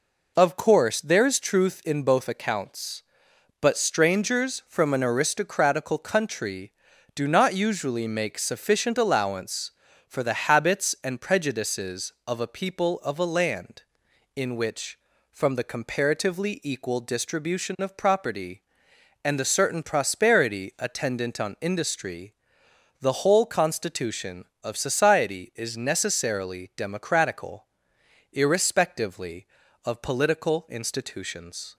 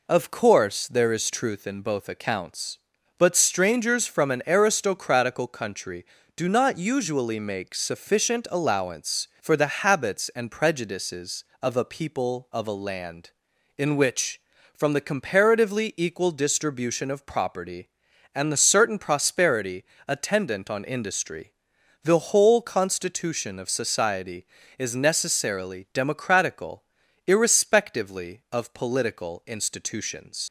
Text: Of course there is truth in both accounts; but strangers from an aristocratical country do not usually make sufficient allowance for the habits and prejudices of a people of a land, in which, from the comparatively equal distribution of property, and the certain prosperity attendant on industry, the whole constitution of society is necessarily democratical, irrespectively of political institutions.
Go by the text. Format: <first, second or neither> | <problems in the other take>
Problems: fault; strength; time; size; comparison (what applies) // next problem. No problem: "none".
first | pauses between "prosperity" and "attendant"; slight; at 19.8 s; 0.22 s long // leaves "institutions" unfinished; at 30.4 s; 75 ms